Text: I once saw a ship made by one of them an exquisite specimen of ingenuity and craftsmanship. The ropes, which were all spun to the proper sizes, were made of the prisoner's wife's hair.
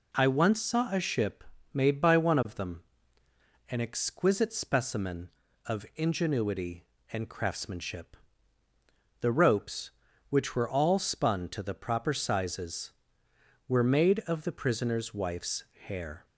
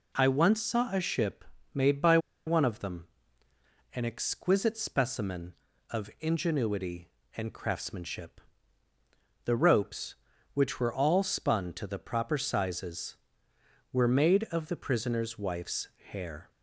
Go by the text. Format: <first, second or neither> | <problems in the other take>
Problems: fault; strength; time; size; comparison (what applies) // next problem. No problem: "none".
first | pauses between "ship" and "made"; slight; at 1.4 s; 0.28 s long; slight in the first // pauses between "by" and "one"; slight; at 2.1 s; 0.28 s long // pauses between "them" and "an"; noticeable; at 3.0 s; 0.88 s long; noticeable in the first // pauses between "wife's" and "hair"; slight; at 15.8 s; 0.22 s long; slight in the first